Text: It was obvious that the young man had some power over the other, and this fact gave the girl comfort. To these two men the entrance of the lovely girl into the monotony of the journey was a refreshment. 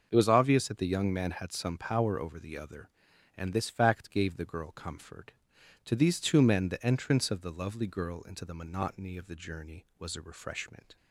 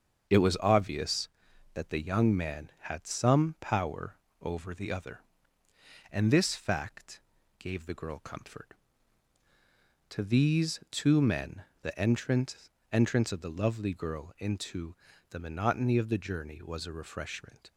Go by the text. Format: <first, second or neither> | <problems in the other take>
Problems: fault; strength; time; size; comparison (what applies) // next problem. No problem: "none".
first | starts louder than the rest; until 1.7 s; 6.5 dB; also in the first // pauses between "power" and "over"; slight; at 4.1 s; 0.24 s long // pauses between "fact" and "gave"; at 7.2 s; 0.38 s long // pauses between "men" and "the"; slight; at 11.6 s; 0.20 s long // says "entrance" twice; at 12.9 s // pauses between "into" and "the"; slight; at 14.9 s; 0.34 s long